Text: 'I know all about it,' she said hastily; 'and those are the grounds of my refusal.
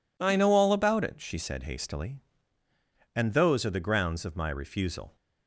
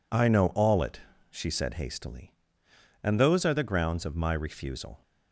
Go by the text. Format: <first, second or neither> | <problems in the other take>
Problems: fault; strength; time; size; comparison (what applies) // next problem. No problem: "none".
first | skips "about"; at 0.8 s